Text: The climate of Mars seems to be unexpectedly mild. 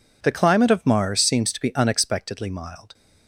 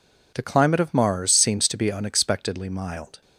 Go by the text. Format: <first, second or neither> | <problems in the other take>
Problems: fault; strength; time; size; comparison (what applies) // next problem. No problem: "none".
neither | none